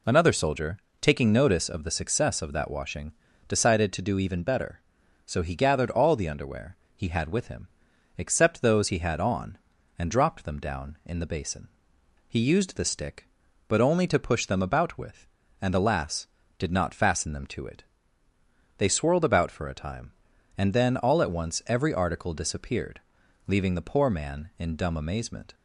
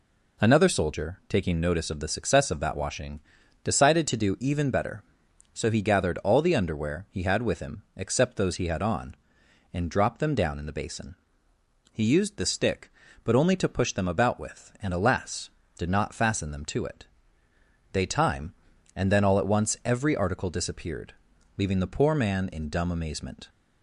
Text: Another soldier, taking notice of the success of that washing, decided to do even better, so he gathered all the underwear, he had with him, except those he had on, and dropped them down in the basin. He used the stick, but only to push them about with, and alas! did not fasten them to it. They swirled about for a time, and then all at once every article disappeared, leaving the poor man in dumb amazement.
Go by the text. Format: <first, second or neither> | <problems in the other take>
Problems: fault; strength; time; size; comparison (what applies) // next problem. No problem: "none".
first | skips "swirled about for a"; at 18.0 s